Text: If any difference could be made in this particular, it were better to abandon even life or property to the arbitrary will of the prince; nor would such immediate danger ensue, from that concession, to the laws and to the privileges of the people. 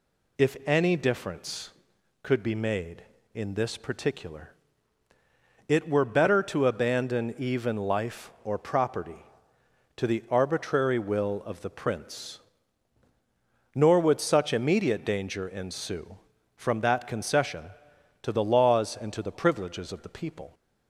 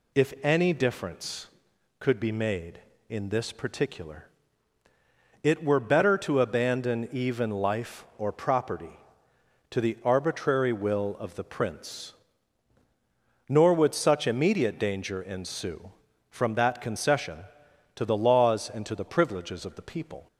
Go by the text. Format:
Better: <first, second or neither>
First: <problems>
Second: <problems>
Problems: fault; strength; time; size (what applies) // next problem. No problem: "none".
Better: neither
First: none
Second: none